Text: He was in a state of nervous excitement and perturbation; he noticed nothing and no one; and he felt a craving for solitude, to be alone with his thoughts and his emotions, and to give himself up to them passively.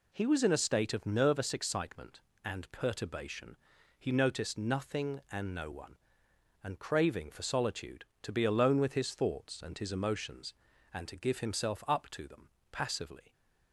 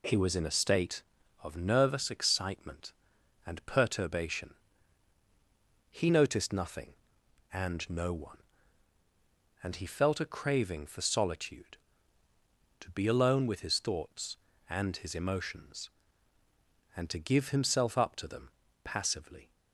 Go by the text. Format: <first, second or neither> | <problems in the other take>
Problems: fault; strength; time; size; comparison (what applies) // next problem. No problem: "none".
second | skips "he felt a"; at 6.7 s // pauses between "them" and "passively"; slight; at 12.4 s; 0.22 s long; slight in the second